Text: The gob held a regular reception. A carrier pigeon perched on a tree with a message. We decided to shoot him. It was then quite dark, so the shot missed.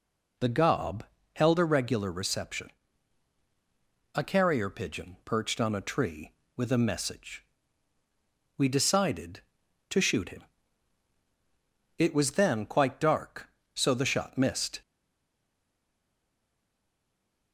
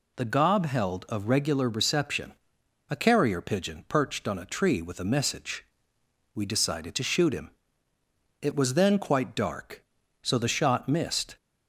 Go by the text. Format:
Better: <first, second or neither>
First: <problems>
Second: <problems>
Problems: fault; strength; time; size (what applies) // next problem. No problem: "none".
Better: second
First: pauses between "gob" and "held"; slight; at 1.0 s; 0.32 s long // stays silent after the last word; strong; from 14.8 s on; 2.7 s long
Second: none